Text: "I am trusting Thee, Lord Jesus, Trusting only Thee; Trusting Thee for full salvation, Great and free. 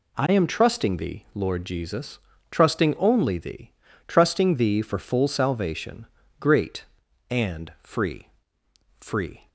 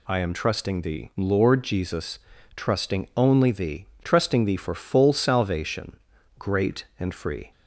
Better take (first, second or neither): second